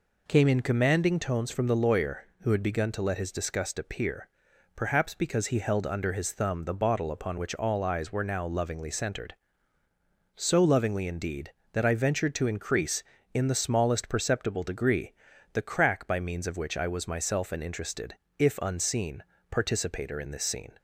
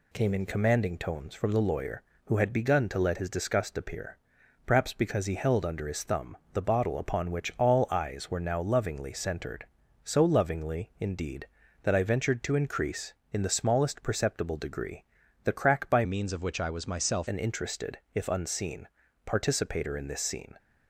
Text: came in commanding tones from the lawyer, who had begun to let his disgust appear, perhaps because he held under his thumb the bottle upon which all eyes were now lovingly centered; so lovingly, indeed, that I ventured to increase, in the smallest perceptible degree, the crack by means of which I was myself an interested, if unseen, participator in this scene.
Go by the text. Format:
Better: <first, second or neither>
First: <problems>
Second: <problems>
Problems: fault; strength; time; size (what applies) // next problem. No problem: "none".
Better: first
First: none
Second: pauses between "thumb" and "the"; slight; at 6.3 s; 0.18 s long // changes voice from "means" to "myself"; from 16.0 to 17.2 s; 1.2 s long